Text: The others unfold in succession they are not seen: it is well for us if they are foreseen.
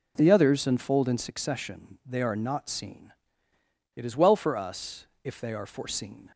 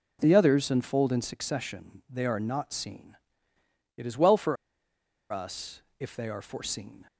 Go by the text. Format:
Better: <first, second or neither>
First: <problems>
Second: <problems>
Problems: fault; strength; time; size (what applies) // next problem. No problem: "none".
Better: first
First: pauses between "us" and "if"; slight; at 5.0 s; 0.16 s long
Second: pauses between "for" and "us"; noticeable; at 4.5 s; 0.76 s long // pauses between "us" and "if"; slight; at 5.8 s; 0.16 s long